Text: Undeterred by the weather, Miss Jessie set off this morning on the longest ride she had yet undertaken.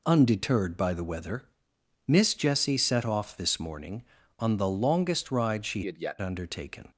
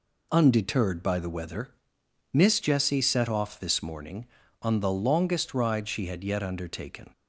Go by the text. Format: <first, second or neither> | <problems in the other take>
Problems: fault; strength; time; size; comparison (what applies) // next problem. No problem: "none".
second | changes voice from "had" to "yet"; from 5.8 to 6.1 s; 0.3 s long